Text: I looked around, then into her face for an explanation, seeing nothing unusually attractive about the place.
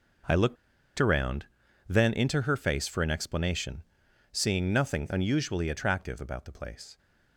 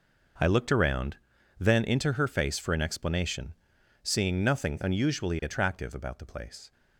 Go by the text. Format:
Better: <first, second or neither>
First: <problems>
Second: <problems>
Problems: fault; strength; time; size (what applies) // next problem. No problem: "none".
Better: second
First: pauses between "looked" and "around"; at 0.5 s; 0.43 s long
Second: none